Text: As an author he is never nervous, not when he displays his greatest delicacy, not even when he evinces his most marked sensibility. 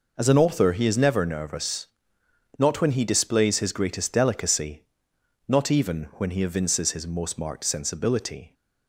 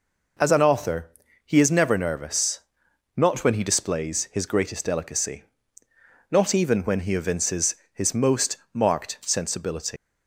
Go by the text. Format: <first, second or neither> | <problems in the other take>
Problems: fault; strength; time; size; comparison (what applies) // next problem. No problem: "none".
first | pauses between "author" and "he"; slight; at 1.0 s; 0.36 s long // pauses between "evinces" and "his"; slight; at 7.7 s; 0.20 s long // pauses between "most" and "marked"; slight; at 8.5 s; 0.16 s long // leaves "sensibility" unfinished; at 9.9 s; 175 ms